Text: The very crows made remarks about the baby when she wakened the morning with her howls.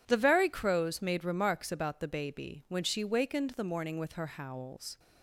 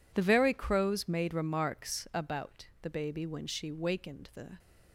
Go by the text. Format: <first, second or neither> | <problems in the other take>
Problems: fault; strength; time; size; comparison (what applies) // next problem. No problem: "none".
first | pauses between "about" and "the"; slight; at 2.6 s; 0.16 s long // stops before "morning with her howls"; at 4.5 s